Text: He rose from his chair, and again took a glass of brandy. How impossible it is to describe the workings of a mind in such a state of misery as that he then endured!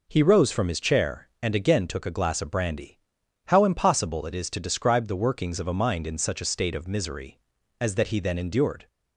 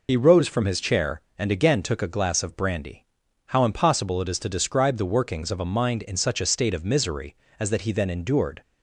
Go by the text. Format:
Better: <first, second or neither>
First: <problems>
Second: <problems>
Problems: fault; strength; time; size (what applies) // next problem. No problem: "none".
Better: first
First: none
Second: loses the start of "He"; at 0.0 s; 50 ms